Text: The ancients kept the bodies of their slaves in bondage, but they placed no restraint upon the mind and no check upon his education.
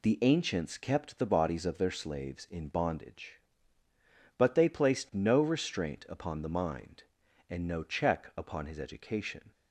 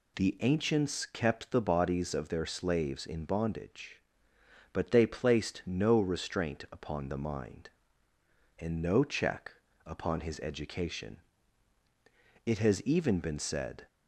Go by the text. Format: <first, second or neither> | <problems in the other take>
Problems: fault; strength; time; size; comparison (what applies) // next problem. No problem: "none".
first | pauses between "check" and "upon"; slight; at 9.5 s; 0.32 s long // goes on to say "It has even been said"; from 12.4 s on; 1.4 s long